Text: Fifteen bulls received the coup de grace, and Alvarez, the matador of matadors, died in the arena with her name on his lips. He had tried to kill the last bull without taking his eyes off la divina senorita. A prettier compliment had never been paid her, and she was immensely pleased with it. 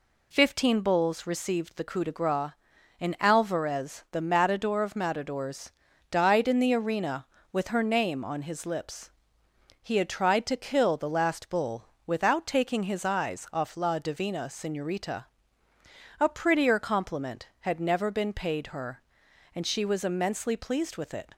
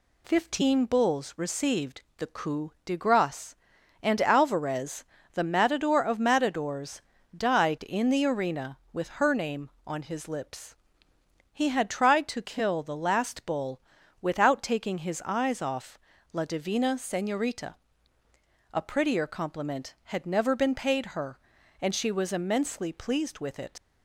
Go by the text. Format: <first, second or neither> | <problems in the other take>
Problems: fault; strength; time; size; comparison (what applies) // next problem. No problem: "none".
first | pauses between "received" and "the"; slight; at 2.0 s; 0.16 s long // pauses between "bull" and "without"; at 13.7 s; 0.40 s long; slight in the first // pauses between "off" and "la"; slight; at 15.9 s; 0.36 s long // leaves "it" unfinished; at 23.7 s; 95 ms